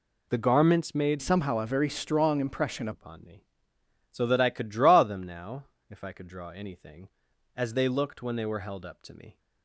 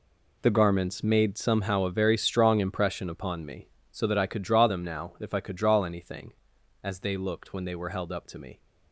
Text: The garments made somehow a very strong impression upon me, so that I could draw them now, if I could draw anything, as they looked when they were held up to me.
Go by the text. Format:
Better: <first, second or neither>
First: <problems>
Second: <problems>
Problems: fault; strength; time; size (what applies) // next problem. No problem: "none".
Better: second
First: changes voice from "somehow" to "impression"; from 1.2 to 2.8 s; 1.6 s long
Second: none